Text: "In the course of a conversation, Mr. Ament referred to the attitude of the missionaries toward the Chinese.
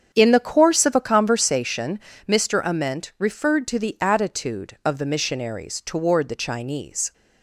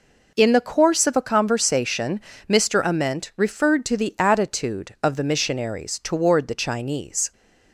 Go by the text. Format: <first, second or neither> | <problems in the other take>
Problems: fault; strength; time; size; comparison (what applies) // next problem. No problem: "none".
second | starts louder than the rest; strong; until 1.6 s; 7.5 dB